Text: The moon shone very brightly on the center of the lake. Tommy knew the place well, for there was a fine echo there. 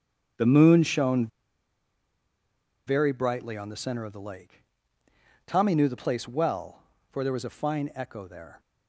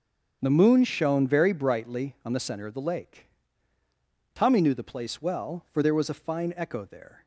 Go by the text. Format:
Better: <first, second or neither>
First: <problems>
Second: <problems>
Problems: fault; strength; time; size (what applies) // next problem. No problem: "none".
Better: second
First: starts louder than the rest; strong; until 2.9 s; 8 dB // pauses between "shone" and "very"; strong; at 1.2 s; 1.5 s long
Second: starts louder than the rest; until 1.4 s; 7 dB